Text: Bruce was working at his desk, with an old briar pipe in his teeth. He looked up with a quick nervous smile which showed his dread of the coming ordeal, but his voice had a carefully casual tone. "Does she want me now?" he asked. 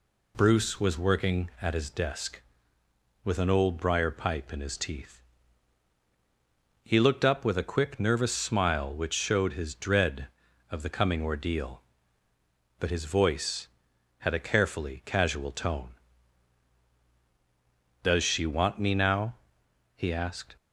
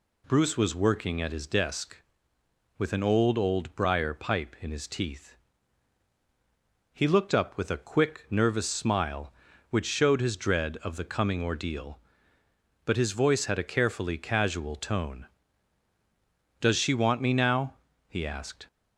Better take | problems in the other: first | says "old" twice; at 3.3 s

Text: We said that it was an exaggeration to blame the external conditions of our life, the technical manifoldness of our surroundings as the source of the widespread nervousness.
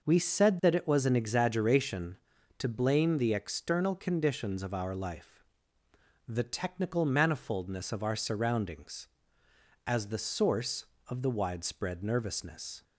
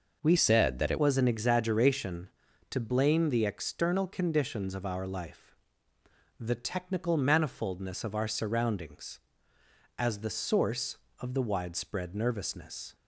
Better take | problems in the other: first | changes voice from "said" to "it"; from 0.3 to 0.9 s; 0.6 s long

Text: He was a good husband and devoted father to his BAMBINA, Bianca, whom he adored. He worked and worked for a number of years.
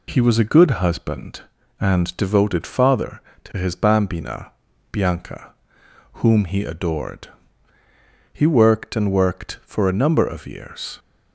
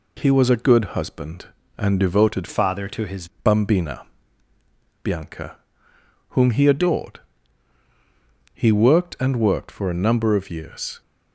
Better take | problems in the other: first | changes voice from "father" to "his"; from 2.4 to 3.2 s; 0.8 s long

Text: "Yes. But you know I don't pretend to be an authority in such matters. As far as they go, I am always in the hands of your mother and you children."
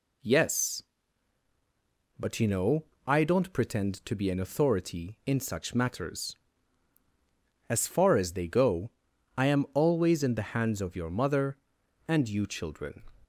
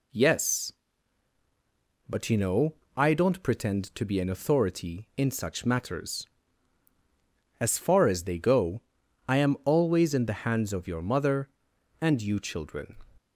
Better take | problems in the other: neither | pauses between "know" and "I"; slight; the same in both

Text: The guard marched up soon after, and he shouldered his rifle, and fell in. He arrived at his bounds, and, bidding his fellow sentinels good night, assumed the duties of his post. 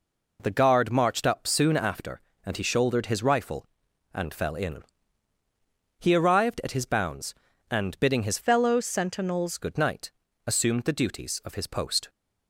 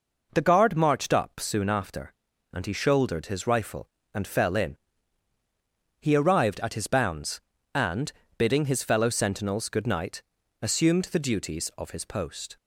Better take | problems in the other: second | changes voice from "fellow" to "sentinels"; from 8.4 to 9.5 s; 1.1 s long

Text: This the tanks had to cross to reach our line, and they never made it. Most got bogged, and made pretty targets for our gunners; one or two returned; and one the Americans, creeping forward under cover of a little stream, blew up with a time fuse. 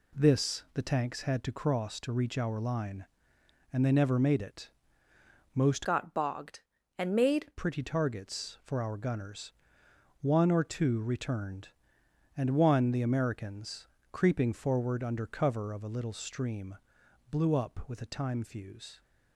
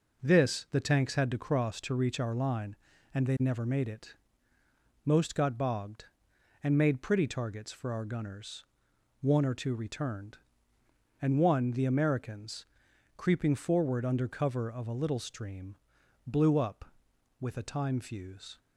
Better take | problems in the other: second | changes voice from "got" to "made"; from 5.8 to 7.5 s; 1.7 s long

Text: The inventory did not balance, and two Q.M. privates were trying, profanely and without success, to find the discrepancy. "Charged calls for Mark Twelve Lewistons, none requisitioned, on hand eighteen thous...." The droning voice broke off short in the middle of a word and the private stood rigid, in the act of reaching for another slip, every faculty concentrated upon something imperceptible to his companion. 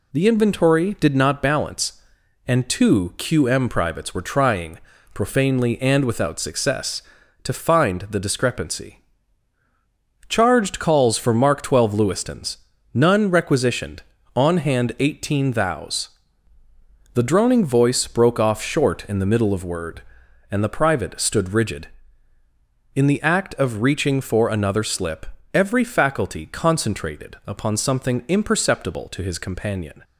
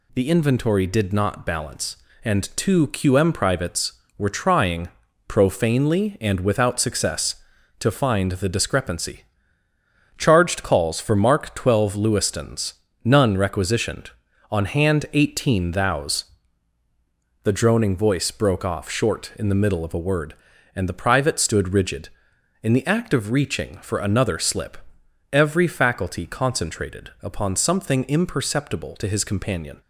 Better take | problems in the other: second | skips "a"; at 19.6 s

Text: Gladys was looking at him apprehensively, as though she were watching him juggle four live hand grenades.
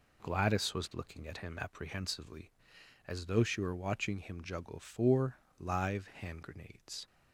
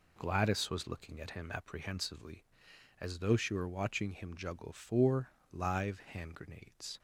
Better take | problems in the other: neither | pauses between "four" and "live"; slight; the same in both

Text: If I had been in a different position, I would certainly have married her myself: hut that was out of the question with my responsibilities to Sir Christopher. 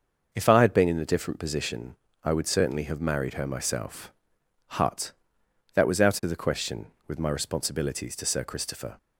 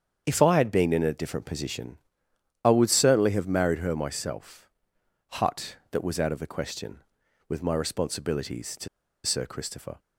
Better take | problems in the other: first | starts louder than the rest; strong; until 1.2 s; 7.5 dB; noticeable in the first // pauses between "to" and "Sir"; at 8.8 s; 0.38 s long

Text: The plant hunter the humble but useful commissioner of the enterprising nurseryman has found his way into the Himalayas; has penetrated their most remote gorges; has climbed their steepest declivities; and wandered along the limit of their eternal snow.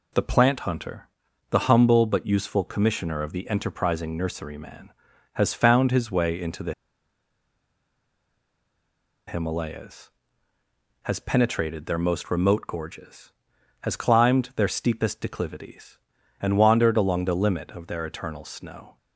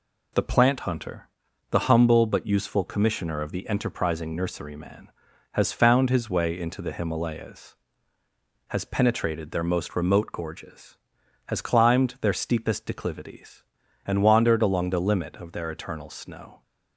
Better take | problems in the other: second | pauses between "hunter" and "the"; at 1.0 s; 0.42 s long; also in the second // pauses between "the" and "Himalayas"; strong; at 6.7 s; 2.5 s long

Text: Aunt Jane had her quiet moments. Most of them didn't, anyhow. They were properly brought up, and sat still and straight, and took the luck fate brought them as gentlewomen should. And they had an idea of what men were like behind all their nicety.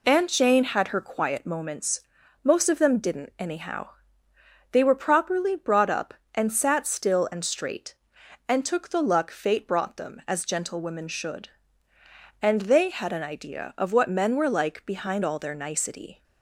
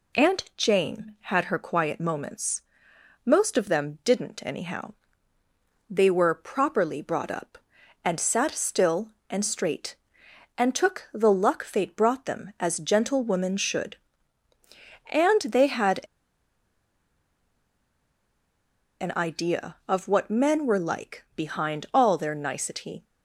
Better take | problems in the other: first | pauses between "had" and "an"; strong; at 15.9 s; 3.0 s long

